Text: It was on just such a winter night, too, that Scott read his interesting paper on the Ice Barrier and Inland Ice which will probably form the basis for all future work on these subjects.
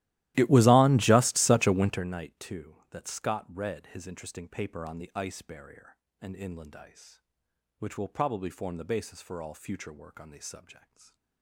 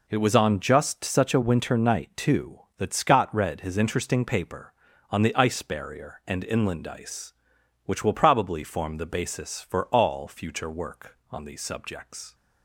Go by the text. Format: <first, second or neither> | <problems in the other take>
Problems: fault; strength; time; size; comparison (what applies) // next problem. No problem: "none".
second | starts louder than the rest; strong; until 2.1 s; 15.5 dB